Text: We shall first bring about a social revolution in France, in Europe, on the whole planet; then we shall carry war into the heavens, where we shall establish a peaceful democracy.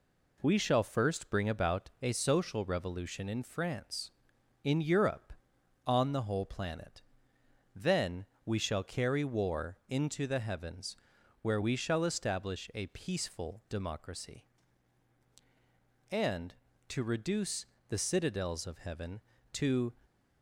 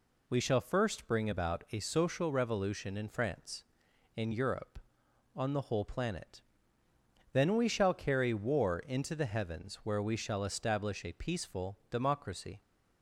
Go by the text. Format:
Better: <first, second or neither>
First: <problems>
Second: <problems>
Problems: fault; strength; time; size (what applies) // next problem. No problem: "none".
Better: second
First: pauses between "then" and "we"; slight; at 8.2 s; 0.20 s long // goes on to say "And to reduce the citadels of Heaven to"; strong; from 16.1 s on; 3.8 s long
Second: none